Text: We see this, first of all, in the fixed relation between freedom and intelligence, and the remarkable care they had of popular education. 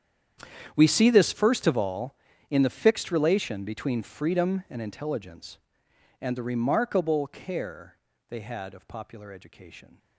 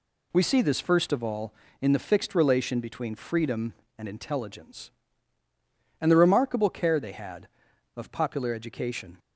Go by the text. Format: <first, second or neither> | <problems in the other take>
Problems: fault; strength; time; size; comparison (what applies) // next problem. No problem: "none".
second | gets quieter; strong; throughout; 18 dB // pauses between "care" and "they"; slight; at 7.9 s; 0.30 s long